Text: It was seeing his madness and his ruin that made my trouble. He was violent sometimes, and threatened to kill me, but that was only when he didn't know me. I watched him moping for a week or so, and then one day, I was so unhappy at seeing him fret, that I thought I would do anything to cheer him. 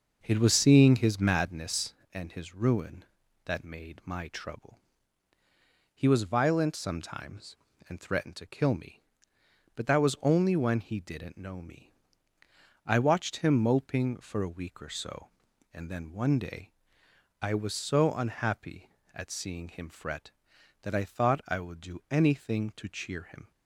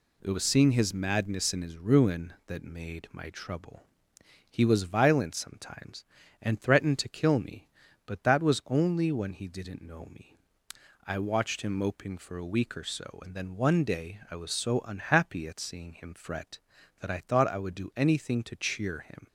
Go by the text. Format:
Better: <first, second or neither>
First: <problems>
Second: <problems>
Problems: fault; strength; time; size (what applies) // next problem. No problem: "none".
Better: second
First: starts louder than the rest; noticeable; until 1.4 s; 6 dB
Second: none